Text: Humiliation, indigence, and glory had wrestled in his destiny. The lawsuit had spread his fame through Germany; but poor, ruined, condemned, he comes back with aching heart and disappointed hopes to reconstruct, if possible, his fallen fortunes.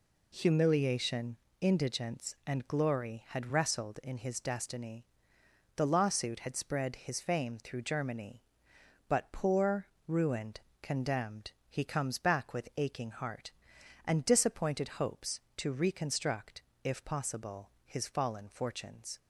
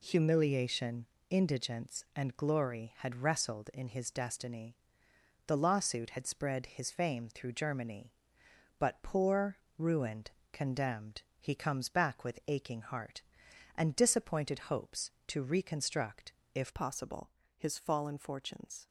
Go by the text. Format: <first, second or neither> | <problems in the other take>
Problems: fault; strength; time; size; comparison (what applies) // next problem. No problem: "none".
first | changes voice at "possible"; from 16.7 s on; 2.1 s long